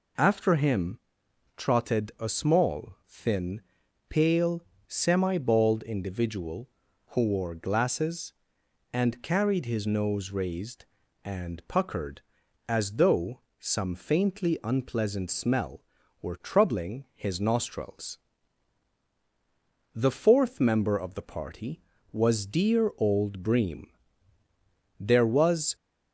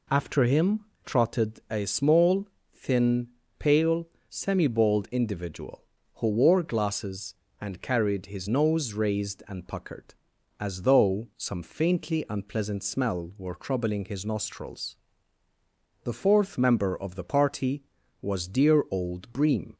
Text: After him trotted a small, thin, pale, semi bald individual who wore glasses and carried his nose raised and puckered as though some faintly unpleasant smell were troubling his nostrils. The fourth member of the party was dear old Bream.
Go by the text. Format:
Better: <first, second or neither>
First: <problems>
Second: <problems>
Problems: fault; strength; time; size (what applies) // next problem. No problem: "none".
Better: second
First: pauses between "him" and "trotted"; noticeable; at 0.9 s; 0.58 s long // pauses between "though" and "some"; slight; at 13.4 s; 0.18 s long // goes on to say "There was"; noticeable; from 24.9 s on; 0.78 s long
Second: pauses between "him" and "trotted"; slight; at 0.8 s; 0.18 s long